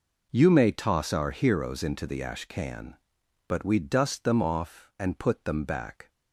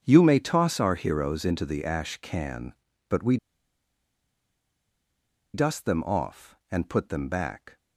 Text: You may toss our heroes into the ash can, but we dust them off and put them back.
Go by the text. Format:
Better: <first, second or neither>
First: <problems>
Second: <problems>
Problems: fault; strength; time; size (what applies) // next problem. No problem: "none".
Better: first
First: none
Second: starts louder than the rest; strong; until 1.0 s; 7 dB // pauses between "we" and "dust"; strong; at 3.3 s; 2.1 s long